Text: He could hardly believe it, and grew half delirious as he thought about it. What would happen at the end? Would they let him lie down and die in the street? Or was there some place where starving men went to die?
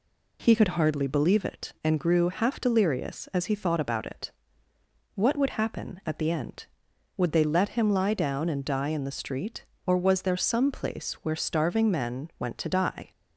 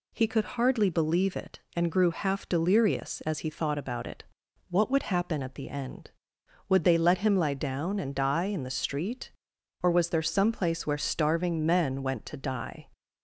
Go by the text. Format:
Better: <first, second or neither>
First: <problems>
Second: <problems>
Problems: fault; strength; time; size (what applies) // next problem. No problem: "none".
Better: neither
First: none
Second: none